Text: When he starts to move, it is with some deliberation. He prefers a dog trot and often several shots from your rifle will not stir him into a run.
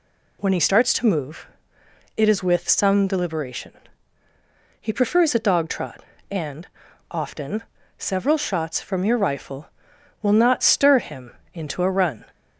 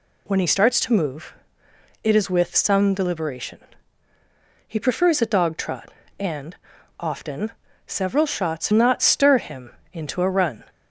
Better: first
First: pauses between "and" and "often"; at 6.6 s; 0.42 s long // pauses between "often" and "several"; slight; at 7.6 s; 0.34 s long // pauses between "him" and "into"; slight; at 11.3 s; 0.22 s long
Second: pauses between "and" and "often"; at 6.5 s; 0.42 s long // pauses between "often" and "several"; slight; at 7.5 s; 0.34 s long // skips "from your rifle will"; at 8.7 s // pauses between "him" and "into"; slight; at 9.7 s; 0.22 s long

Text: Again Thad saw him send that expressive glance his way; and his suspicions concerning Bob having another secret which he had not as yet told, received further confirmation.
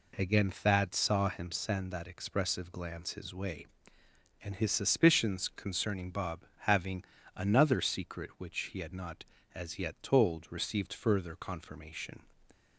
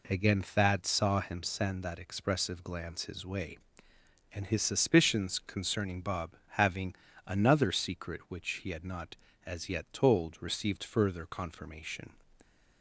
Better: neither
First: pauses between "Bob" and "having"; slight; at 6.4 s; 0.26 s long // pauses between "having" and "another"; slight; at 7.0 s; 0.32 s long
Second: pauses between "Bob" and "having"; slight; at 6.3 s; 0.26 s long // pauses between "having" and "another"; slight; at 6.9 s; 0.32 s long

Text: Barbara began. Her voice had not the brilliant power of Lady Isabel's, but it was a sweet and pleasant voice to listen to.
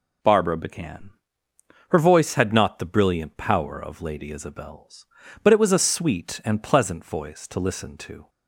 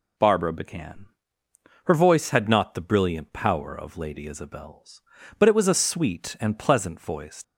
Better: first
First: none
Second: stops before "to listen to"; at 7.4 s

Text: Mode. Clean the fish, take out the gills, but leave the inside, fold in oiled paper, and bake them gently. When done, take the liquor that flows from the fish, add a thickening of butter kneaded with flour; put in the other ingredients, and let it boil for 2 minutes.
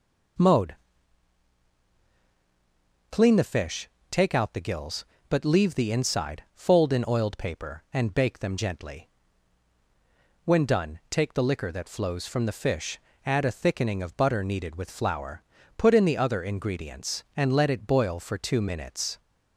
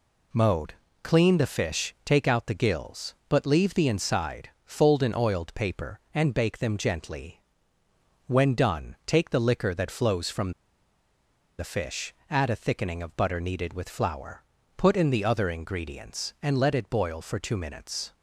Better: first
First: none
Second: pauses between "from" and "the"; at 10.5 s; 1.0 s long

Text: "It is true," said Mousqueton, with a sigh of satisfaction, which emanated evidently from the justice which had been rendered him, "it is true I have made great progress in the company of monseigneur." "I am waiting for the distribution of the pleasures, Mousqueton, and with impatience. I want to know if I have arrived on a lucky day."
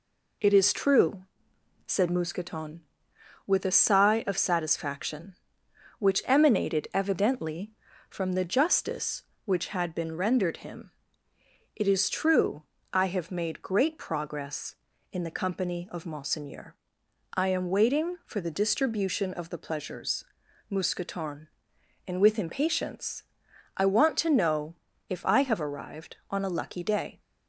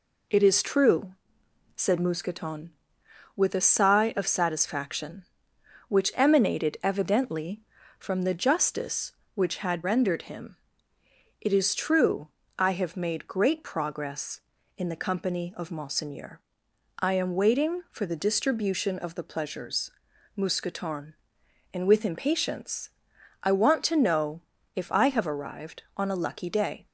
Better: first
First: pauses between "true" and "I"; slight; at 12.6 s; 0.30 s long // pauses between "know" and "if"; slight; at 24.7 s; 0.34 s long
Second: skips "been"; at 9.8 s // pauses between "true" and "I"; slight; at 12.2 s; 0.30 s long // pauses between "know" and "if"; slight; at 24.3 s; 0.34 s long

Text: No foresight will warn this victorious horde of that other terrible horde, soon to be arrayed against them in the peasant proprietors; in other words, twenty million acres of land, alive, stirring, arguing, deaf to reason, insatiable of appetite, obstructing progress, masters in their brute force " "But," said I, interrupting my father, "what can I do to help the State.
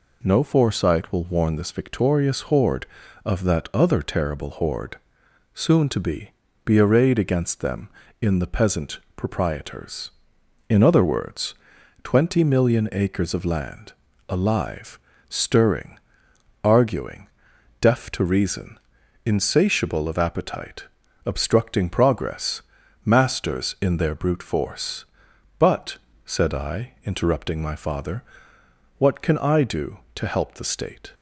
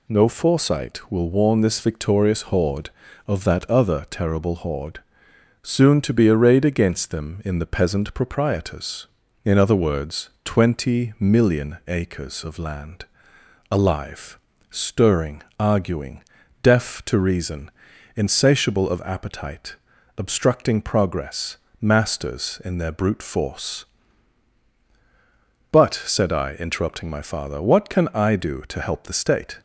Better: second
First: says "be" twice; at 6.6 s // pauses between "peasant" and "proprietors"; slight; at 8.9 s; 0.16 s long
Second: none

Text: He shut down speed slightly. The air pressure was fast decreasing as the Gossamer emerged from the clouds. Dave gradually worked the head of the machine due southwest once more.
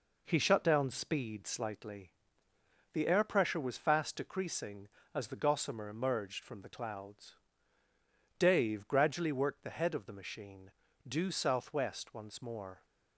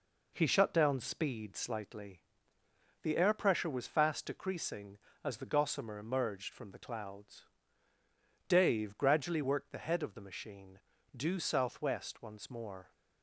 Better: neither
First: pauses between "machine" and "due"; slight; at 10.7 s; 0.36 s long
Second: pauses between "machine" and "due"; slight; at 10.7 s; 0.36 s long

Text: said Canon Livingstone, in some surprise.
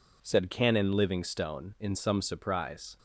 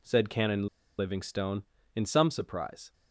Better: first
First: none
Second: pauses between "Canon" and "Livingstone"; slight; at 0.6 s; 0.32 s long

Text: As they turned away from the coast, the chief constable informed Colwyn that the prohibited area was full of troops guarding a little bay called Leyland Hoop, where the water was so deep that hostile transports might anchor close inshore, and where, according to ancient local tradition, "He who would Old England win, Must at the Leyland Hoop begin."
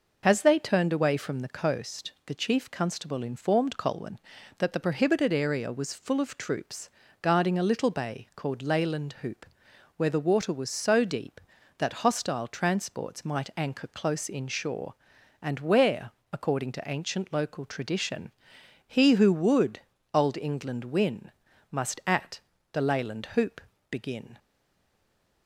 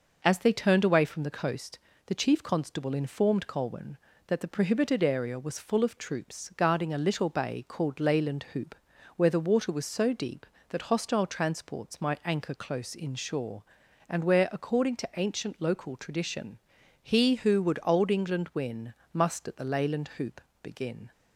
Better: second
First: pauses between "troops" and "guarding"; slight; at 6.8 s; 0.32 s long // pauses between "would" and "Old"; slight; at 19.8 s; 0.34 s long // pauses between "at" and "the"; slight; at 22.4 s; 0.32 s long // pauses between "Hoop" and "begin"; slight; at 23.6 s; 0.30 s long // stays silent after the last word; from 24.3 s on; 1.1 s long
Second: pauses between "Hoop" and "begin"; slight; at 20.4 s; 0.22 s long

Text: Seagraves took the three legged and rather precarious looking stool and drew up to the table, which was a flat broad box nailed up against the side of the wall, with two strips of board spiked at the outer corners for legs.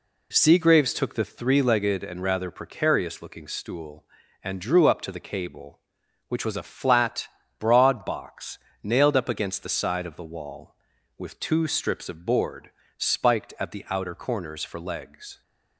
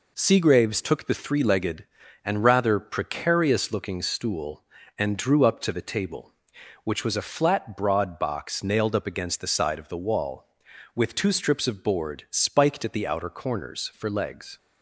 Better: second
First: says "cable" for "table"; at 5.1 s // pauses between "flat" and "broad"; slight; at 7.2 s; 0.32 s long // pauses between "box" and "nailed"; slight; at 8.5 s; 0.24 s long // pauses between "board" and "spiked"; slight; at 12.6 s; 0.26 s long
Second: none

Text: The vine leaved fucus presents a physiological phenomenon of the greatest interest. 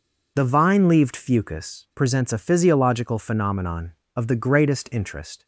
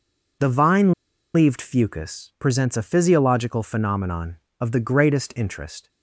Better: first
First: none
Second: pauses between "vine" and "leaved"; at 0.9 s; 0.43 s long

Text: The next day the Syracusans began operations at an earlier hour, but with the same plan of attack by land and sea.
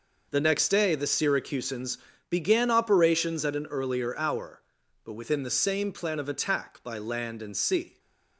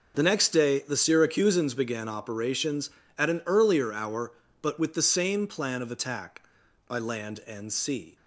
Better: second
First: pauses between "Syracusans" and "began"; slight; at 1.9 s; 0.32 s long // says "within" for "with"; at 5.1 s // stays silent after the last word; slight; from 7.8 s on; 0.5 s long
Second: none

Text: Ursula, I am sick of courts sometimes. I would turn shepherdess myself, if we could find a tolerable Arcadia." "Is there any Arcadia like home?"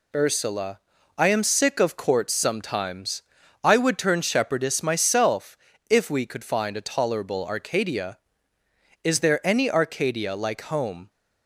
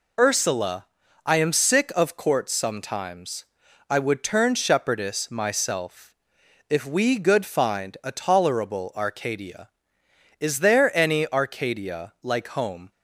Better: first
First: none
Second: says "good" for "could"; at 7.1 s

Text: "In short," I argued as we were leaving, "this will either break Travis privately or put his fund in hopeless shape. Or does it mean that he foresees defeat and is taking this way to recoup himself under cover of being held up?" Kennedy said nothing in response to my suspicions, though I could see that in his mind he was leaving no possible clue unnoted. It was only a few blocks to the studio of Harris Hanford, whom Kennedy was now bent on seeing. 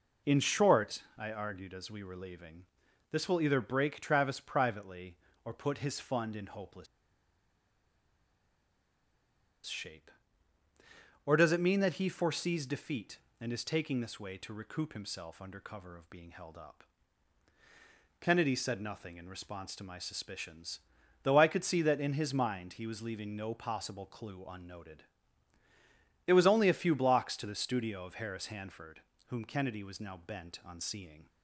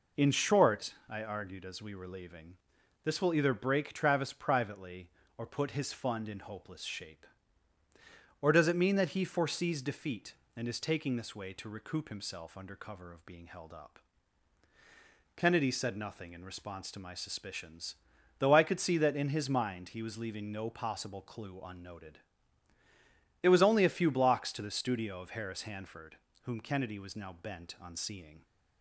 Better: second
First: pauses between "hopeless" and "shape"; strong; at 6.8 s; 2.8 s long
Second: none

